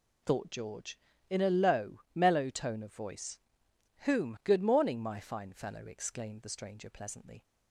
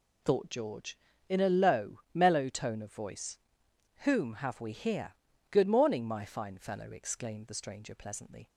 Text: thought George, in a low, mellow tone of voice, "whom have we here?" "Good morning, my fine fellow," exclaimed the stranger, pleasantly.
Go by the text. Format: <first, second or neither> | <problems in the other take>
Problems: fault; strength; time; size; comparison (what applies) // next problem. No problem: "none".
second | skips "have we here"; at 4.3 s